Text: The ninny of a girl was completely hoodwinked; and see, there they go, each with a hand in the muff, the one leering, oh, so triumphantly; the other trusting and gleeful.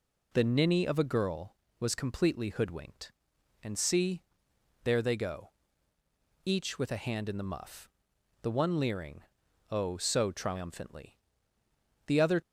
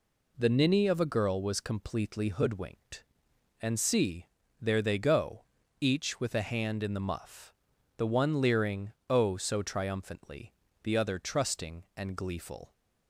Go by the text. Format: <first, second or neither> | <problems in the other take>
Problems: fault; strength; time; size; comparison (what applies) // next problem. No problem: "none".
second | stops before "trusting and gleeful"; at 12.4 s